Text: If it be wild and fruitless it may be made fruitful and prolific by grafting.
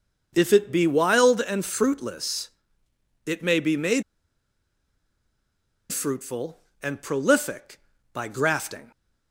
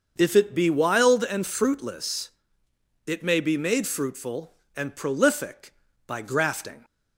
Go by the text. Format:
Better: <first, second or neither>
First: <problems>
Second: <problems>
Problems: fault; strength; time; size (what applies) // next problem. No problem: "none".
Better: second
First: starts louder than the rest; until 1.3 s; 6.5 dB // pauses between "fruitless" and "it"; noticeable; at 2.4 s; 0.76 s long // pauses between "made" and "fruitful"; strong; at 4.0 s; 1.8 s long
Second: starts louder than the rest; until 1.1 s; 6.5 dB // pauses between "fruitless" and "it"; noticeable; at 2.3 s; 0.76 s long